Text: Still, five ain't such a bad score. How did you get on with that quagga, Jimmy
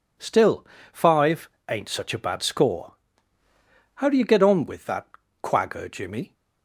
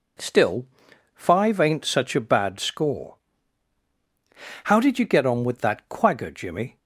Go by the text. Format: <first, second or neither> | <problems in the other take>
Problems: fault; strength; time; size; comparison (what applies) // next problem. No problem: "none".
second | pauses between "five" and "ain't"; slight; at 1.4 s; 0.20 s long // says "do" for "did"; at 4.0 s // pauses between "that" and "quagga"; slight; at 5.0 s; 0.36 s long